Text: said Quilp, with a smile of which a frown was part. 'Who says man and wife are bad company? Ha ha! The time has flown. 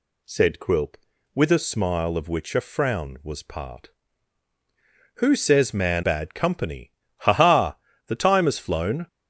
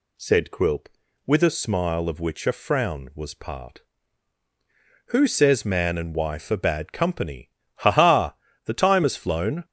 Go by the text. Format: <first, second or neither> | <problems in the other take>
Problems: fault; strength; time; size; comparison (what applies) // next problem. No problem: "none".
second | skips "and wife are"; at 6.0 s